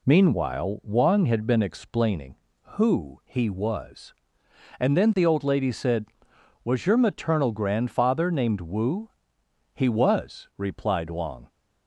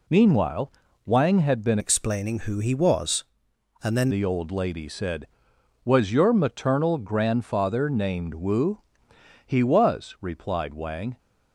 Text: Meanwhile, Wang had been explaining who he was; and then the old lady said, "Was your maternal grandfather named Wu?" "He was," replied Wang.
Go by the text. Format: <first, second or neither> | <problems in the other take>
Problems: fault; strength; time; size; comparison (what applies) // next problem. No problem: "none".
first | changes voice from "explaining" to "then"; from 1.7 to 4.0 s; 2.3 s long